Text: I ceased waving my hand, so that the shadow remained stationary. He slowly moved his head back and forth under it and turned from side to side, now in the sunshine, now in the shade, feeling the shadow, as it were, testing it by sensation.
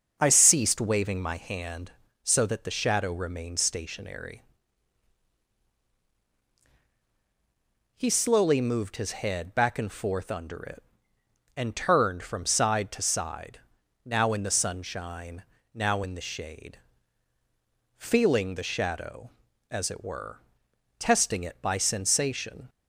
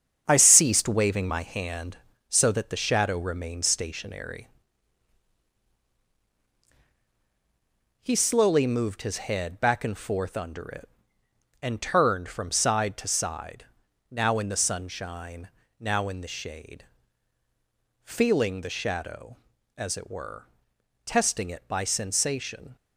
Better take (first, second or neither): first